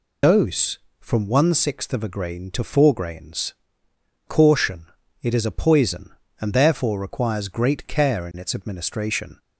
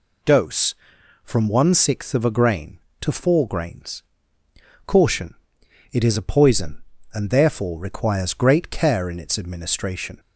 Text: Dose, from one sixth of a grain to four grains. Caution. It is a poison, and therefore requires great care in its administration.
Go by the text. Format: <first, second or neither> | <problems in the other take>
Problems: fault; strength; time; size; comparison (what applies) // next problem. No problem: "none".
second | loses the start of "Dose"; at 0.2 s; 85 ms